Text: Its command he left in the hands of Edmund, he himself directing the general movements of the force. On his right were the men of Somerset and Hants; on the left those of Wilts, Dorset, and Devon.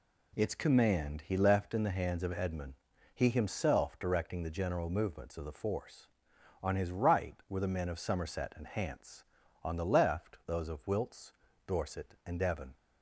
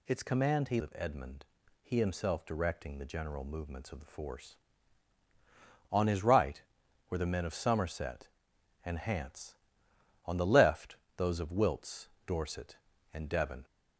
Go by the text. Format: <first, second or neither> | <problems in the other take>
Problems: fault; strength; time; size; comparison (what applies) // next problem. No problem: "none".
first | skips "left in the hands"; at 0.7 s // pauses between "left" and "those"; slight; at 10.9 s; 0.22 s long